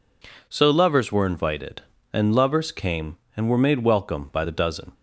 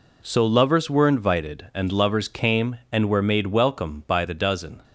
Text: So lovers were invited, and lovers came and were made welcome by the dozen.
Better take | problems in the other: neither | none

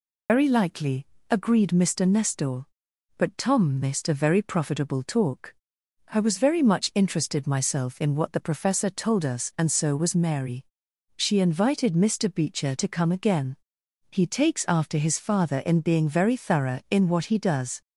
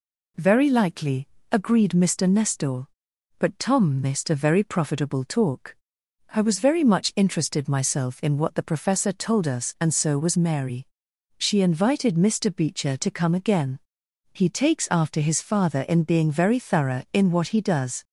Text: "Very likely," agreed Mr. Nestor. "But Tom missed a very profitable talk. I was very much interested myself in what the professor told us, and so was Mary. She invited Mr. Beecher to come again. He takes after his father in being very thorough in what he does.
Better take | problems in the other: second | loses the start of "Very"; at 0.2 s; 150 ms

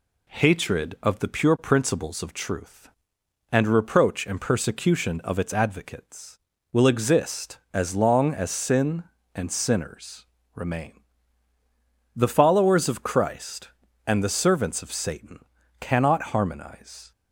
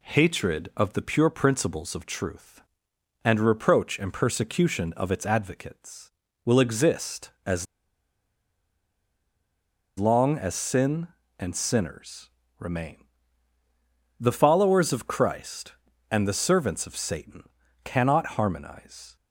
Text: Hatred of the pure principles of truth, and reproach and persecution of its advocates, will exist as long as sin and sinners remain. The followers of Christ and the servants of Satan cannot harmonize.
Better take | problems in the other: first | pauses between "as" and "long"; strong; at 7.6 s; 2.3 s long // pauses between "sinners" and "remain"; slight; at 12.2 s; 0.28 s long; slight in the first // pauses between "Satan" and "cannot"; at 17.4 s; 0.40 s long; also in the first

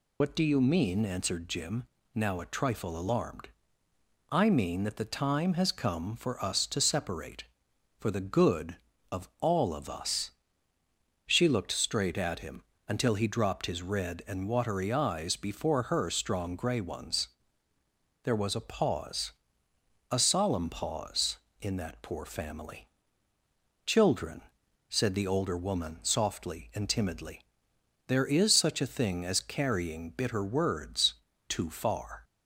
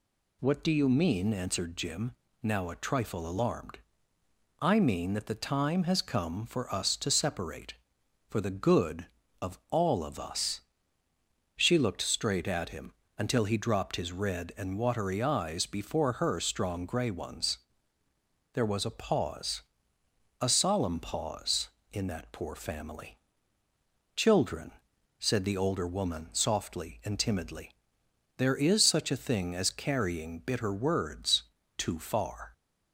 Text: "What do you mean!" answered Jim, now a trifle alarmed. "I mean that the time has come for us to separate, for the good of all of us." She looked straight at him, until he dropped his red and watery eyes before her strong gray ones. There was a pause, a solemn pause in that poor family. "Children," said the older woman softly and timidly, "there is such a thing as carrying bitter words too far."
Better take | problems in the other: second | loses the start of "What"; at 0.2 s; 70 ms // pauses between "words" and "too"; slight; at 31.1 s; 0.34 s long; slight in the second

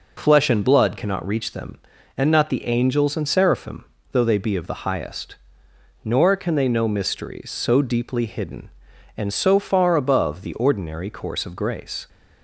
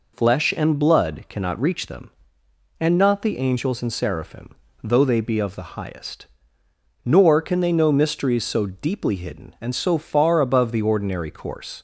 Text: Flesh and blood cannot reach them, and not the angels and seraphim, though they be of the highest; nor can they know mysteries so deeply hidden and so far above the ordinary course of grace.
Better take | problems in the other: first | stops before "of grace"; at 11.7 s

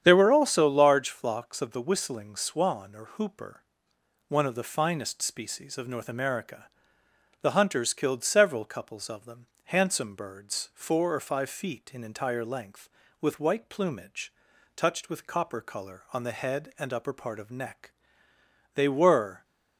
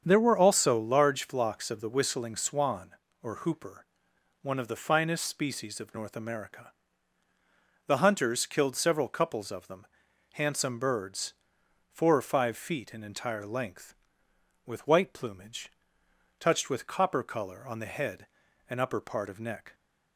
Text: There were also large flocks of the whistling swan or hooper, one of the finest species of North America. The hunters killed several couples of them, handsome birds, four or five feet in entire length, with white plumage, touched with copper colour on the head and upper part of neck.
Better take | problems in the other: second | starts louder than the rest; strong; until 1.0 s; 9 dB; strong in the second // goes on to say "They were"; noticeable; from 18.7 s on; 0.70 s long

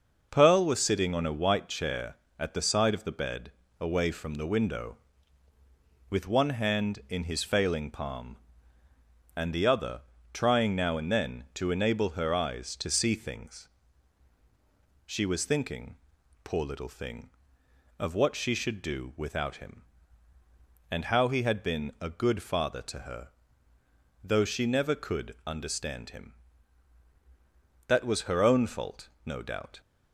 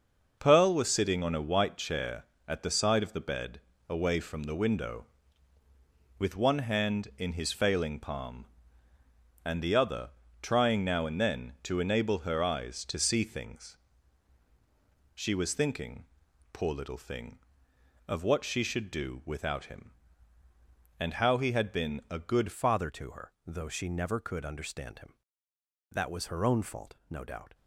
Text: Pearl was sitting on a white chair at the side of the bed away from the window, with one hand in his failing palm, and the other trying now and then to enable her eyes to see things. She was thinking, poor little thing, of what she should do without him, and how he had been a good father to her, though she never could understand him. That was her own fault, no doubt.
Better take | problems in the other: first | starts louder than the rest; noticeable; until 1.4 s; 6 dB; noticeable in the first // pauses between "bed" and "away"; slight; at 3.5 s; 0.28 s long; slight in the first // pauses between "other" and "trying"; slight; at 10.0 s; 0.32 s long; slight in the first // changes voice at "father"; from 22.5 s on; 5.0 s long

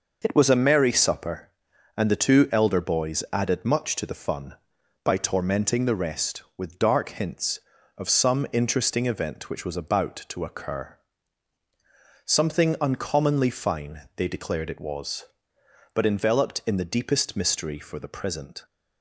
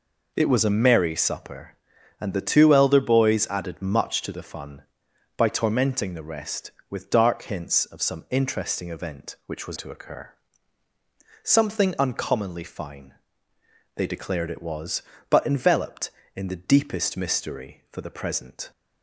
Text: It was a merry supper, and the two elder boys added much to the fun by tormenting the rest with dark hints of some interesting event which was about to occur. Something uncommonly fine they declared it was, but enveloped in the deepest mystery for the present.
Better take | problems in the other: first | skips "about"; at 9.7 s // pauses between "fine" and "they"; noticeable; at 13.1 s; 0.82 s long

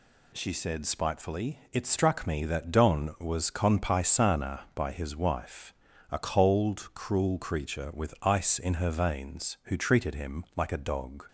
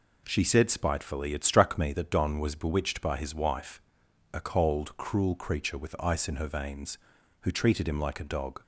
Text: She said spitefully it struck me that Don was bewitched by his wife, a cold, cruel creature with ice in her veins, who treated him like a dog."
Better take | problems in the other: second | says "conpaisana" for "bewitched"; at 3.5 s

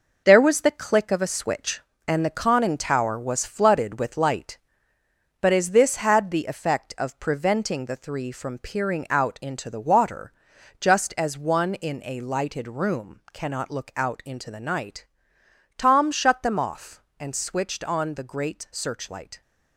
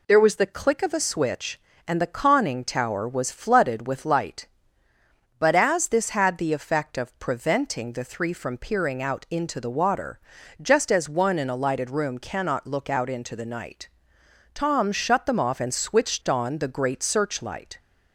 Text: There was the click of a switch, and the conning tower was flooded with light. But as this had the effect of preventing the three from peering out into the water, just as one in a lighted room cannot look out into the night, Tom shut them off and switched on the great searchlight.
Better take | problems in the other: second | gets quieter; strong; throughout; 7.5 dB

